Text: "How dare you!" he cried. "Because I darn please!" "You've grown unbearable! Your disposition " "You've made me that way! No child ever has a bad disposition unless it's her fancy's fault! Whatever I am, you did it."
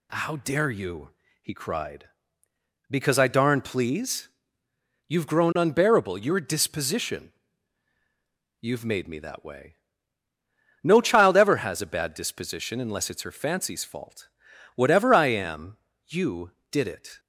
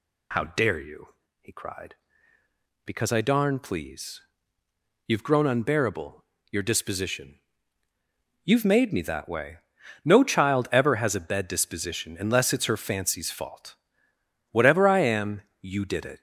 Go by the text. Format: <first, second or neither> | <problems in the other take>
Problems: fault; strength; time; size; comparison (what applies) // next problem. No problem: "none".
first | says "bed" for "bad"; at 11.2 s